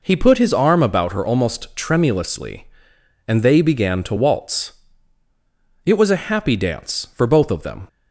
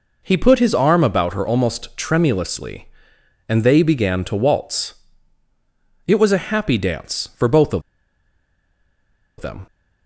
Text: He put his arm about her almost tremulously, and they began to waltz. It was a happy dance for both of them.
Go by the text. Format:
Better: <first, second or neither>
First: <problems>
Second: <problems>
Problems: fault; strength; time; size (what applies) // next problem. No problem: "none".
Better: first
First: none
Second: pauses between "of" and "them"; strong; at 7.8 s; 1.5 s long